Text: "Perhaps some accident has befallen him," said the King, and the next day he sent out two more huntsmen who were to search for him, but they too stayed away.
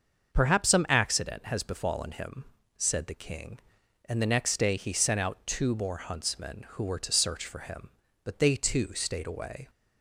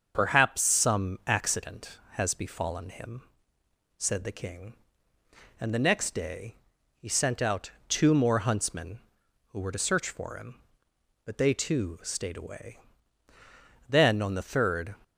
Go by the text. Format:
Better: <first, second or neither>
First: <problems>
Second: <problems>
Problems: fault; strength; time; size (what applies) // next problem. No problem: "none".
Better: first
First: starts louder than the rest; until 1.3 s; 6.5 dB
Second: starts louder than the rest; until 1.1 s; 6.5 dB // pauses between "day" and "he"; at 6.5 s; 0.40 s long // pauses between "out" and "two"; slight; at 7.7 s; 0.18 s long // goes on to say "Then on the third"; noticeable; from 13.8 s on; 1.0 s long